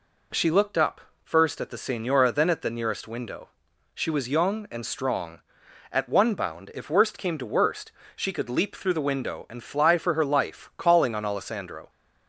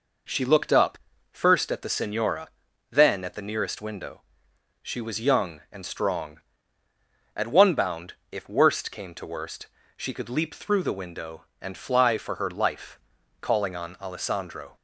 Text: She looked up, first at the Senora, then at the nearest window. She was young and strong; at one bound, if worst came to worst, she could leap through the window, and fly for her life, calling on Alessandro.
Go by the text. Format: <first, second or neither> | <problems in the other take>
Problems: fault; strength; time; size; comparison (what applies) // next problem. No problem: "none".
neither | none